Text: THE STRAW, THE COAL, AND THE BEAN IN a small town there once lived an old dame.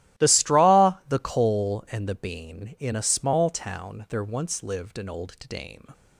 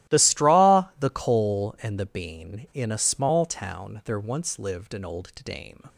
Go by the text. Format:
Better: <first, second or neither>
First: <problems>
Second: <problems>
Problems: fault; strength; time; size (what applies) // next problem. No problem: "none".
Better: neither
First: starts louder than the rest; strong; until 1.3 s; 16.5 dB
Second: starts louder than the rest; strong; until 1.2 s; 16.5 dB